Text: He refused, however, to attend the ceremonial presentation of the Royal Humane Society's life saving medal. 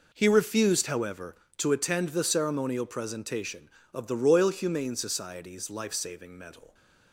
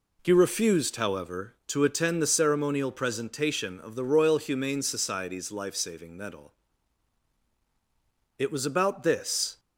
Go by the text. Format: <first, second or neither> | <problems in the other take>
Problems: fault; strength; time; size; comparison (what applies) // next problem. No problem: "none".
first | goes on to say "It was about this"; noticeable; from 8.3 s on; 1.2 s long